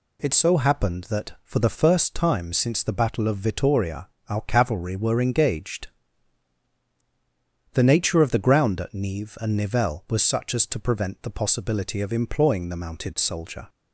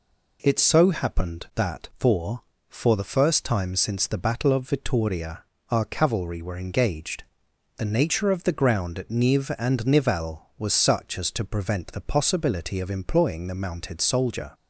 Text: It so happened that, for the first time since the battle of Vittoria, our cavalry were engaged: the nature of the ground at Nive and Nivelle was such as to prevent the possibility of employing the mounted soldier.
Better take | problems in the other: first | says "for" twice; at 2.6 s

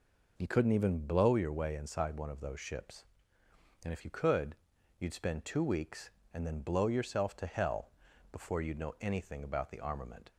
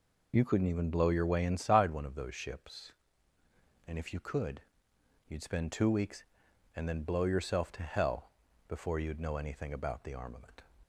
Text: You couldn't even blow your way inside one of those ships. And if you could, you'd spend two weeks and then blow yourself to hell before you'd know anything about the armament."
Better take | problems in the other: neither | pauses between "hell" and "before"; the same in both

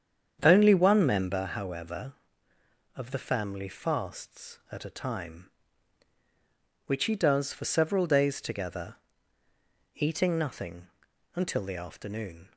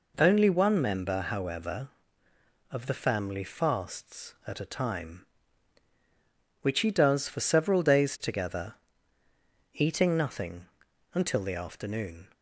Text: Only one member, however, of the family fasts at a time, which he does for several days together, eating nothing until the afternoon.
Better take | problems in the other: second | starts louder than the rest; strong; until 1.4 s; 8 dB // pauses between "nothing" and "until"; noticeable; at 10.8 s; 0.48 s long; noticeable in the second

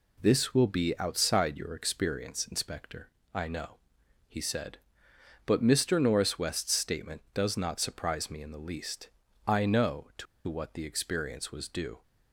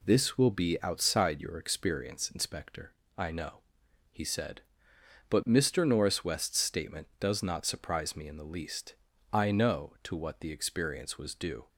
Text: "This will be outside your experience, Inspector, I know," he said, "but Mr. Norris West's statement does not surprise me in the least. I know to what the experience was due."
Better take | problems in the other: second | pauses between "to" and "what"; slight; at 10.2 s; 0.22 s long

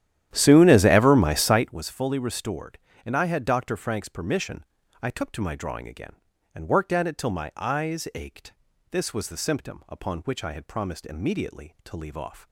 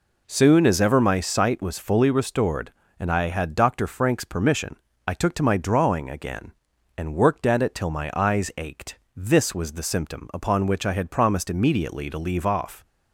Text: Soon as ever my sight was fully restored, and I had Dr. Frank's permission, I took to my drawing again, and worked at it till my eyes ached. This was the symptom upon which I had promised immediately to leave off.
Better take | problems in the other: second | starts louder than the rest; strong; until 1.8 s; 11.5 dB

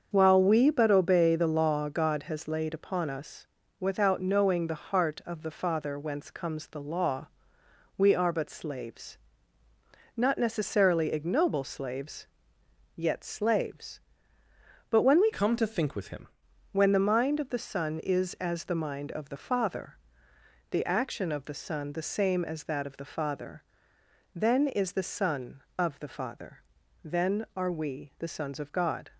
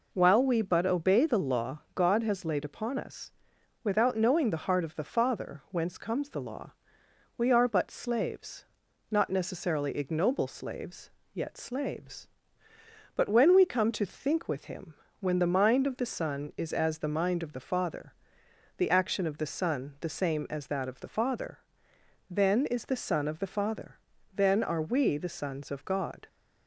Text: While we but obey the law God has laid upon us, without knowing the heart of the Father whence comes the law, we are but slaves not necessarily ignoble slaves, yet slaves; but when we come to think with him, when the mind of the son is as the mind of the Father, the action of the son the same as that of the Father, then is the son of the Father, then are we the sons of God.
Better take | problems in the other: second | starts louder than the rest; until 1.1 s; 7 dB // pauses between "slaves" and "not"; noticeable; at 9.1 s; 0.96 s long; noticeable in the second // changes voice from "come" to "him"; from 15.3 to 16.2 s; 0.9 s long

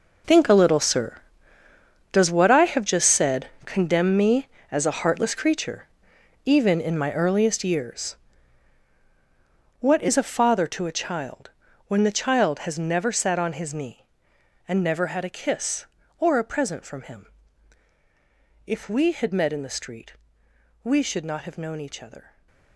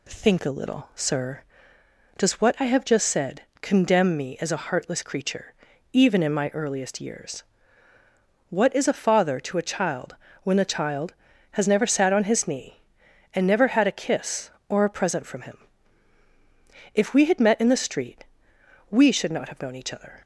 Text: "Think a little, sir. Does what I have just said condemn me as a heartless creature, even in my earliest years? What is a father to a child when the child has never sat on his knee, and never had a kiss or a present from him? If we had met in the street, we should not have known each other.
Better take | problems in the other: second | gets quieter; strong; throughout; 14 dB // pauses between "said" and "condemn"; slight; at 3.4 s; 0.18 s long; slight in the second // pauses between "child" and "when"; at 11.5 s; 0.38 s long; slight in the second

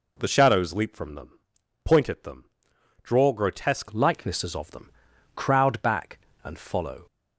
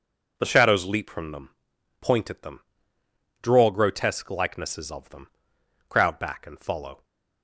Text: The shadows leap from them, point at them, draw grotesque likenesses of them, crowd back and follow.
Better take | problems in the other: second | changes voice at "likenesses"; from 3.9 s on; 3.1 s long

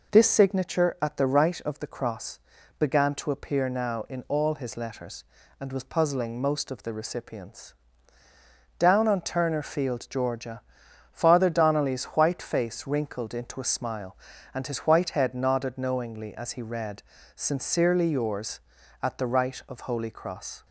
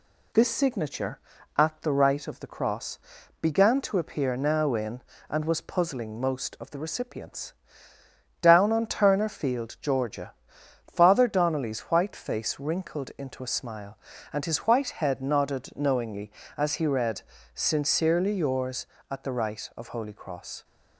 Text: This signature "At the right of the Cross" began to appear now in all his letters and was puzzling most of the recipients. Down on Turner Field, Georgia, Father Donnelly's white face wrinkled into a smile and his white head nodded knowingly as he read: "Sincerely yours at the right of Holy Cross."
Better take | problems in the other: first | pauses between "Cross" and "began"; at 2.9 s; 0.42 s long; also in the first // skips "all his letters"; at 5.1 s

